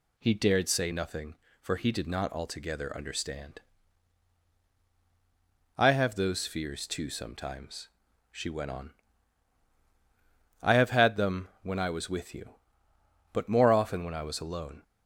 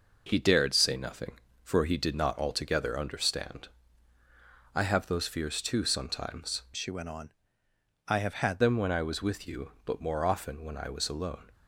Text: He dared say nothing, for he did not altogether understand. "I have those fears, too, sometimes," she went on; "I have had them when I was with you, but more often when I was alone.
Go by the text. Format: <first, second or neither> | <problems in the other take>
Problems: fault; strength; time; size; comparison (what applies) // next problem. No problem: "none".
first | changes voice from "she" to "had"; from 6.7 to 8.5 s; 1.8 s long